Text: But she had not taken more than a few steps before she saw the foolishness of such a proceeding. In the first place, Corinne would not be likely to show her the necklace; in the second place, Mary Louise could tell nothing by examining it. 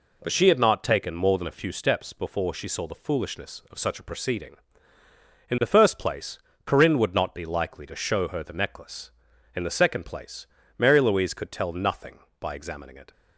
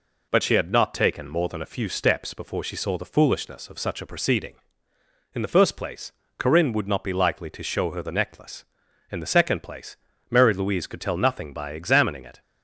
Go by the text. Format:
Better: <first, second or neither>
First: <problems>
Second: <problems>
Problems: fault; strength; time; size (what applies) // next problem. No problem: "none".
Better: neither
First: none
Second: none